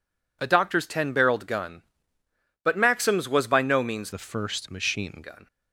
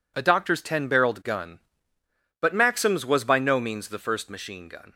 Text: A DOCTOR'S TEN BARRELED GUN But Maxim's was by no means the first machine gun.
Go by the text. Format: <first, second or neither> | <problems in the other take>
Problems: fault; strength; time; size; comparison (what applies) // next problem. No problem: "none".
second | changes voice from "the" to "machine"; from 4.1 to 5.1 s; 1.0 s long